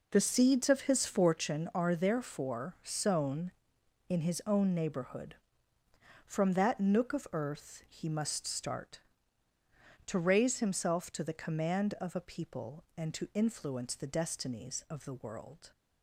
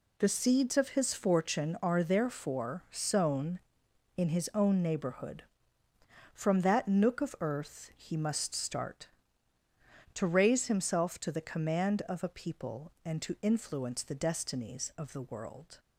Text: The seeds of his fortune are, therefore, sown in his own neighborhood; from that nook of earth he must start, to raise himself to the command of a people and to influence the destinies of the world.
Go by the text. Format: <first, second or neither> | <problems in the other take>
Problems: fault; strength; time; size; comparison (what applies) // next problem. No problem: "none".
second | starts louder than the rest; noticeable; until 1.4 s; 4.5 dB